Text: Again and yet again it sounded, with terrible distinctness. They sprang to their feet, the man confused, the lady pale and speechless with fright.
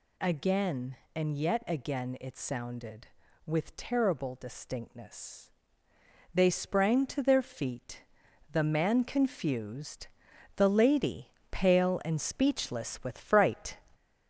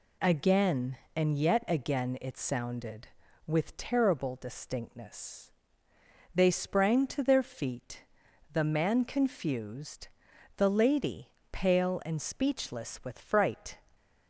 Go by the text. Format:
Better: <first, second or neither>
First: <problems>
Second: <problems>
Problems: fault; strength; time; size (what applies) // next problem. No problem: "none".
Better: second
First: gets louder; noticeable; throughout; 4 dB // pauses between "lady" and "pale"; slight; at 11.2 s; 0.24 s long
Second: pauses between "lady" and "pale"; slight; at 11.2 s; 0.24 s long